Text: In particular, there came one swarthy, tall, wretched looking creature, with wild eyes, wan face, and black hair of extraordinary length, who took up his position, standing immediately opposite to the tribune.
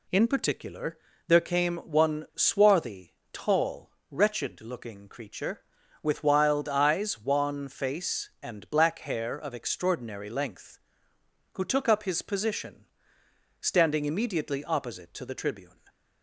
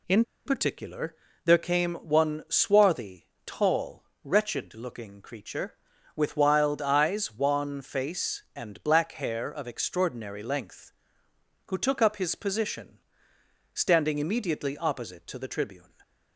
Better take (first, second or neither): first